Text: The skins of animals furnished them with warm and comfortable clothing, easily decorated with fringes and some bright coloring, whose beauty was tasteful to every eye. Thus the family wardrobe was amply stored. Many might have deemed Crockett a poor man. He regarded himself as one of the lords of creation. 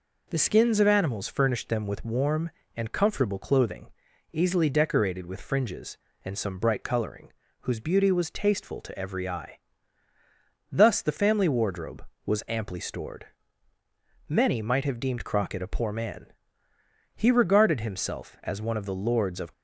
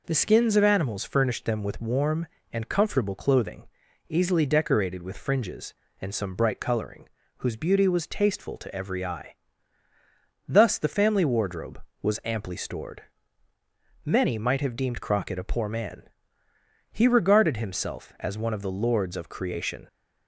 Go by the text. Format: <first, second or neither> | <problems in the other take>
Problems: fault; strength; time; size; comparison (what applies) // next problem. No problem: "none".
second | stops before "creation"; at 19.5 s